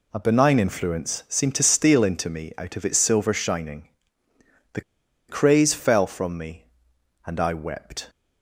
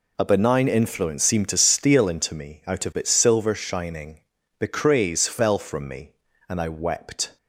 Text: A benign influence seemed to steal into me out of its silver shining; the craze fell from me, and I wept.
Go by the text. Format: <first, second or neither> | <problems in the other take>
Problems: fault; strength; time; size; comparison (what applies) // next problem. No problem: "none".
second | pauses between "the" and "craze"; noticeable; at 4.7 s; 0.48 s long